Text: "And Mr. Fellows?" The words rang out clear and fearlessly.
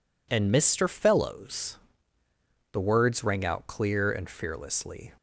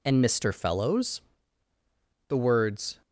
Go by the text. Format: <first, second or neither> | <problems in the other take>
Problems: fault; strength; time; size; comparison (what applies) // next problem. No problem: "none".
first | stops before "rang out clear and fearlessly"; at 3.0 s